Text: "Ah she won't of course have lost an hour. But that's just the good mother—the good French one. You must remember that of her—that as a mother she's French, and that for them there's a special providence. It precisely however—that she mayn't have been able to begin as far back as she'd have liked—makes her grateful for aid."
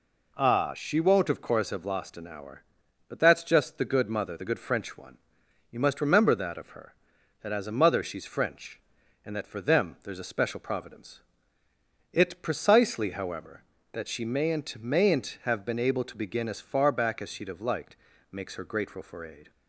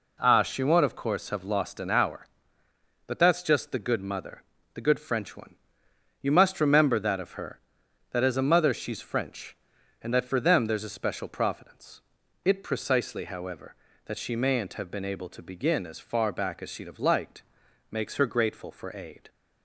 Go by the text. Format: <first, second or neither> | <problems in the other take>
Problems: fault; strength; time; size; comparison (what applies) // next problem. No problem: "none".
second | says "mayn't" twice; at 14.8 s